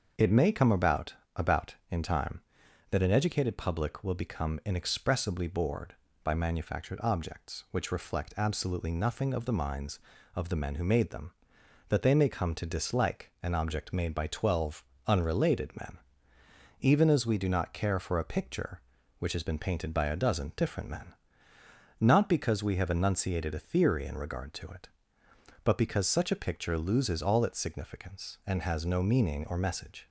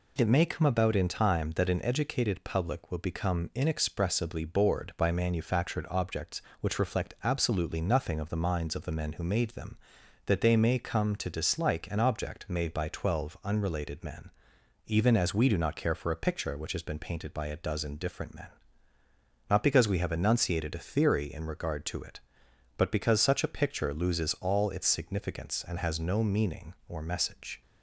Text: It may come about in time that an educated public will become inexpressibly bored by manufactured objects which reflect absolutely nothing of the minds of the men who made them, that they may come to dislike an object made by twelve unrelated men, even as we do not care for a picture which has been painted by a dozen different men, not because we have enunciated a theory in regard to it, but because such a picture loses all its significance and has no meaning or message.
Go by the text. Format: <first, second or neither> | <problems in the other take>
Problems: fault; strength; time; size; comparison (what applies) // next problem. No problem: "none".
second | starts louder than the rest; until 1.4 s; 6.5 dB // says "about" twice; at 1.3 s // pauses between "twelve" and "unrelated"; slight; at 14.8 s; 0.24 s long